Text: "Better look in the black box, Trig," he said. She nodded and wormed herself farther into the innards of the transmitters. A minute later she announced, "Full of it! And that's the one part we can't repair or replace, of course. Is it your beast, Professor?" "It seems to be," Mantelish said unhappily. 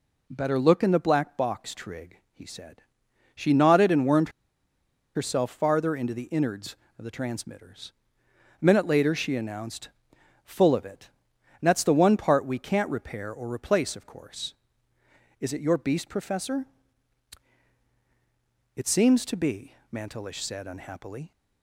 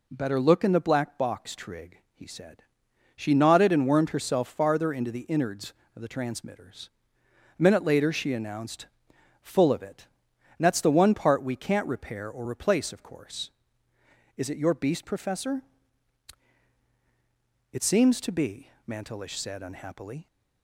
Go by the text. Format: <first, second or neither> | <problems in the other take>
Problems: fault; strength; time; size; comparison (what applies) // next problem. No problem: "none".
second | pauses between "wormed" and "herself"; noticeable; at 4.2 s; 0.85 s long